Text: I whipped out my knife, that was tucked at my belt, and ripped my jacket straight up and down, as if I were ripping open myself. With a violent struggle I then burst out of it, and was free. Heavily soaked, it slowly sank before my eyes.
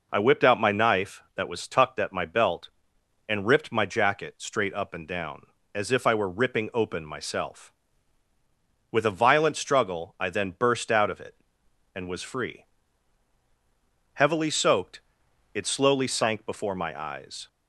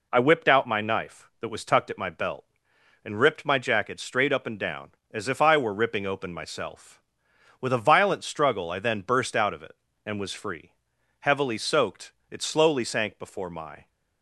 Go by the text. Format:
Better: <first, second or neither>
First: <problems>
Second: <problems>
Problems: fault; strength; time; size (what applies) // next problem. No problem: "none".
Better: first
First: none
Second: stops before "eyes"; at 13.8 s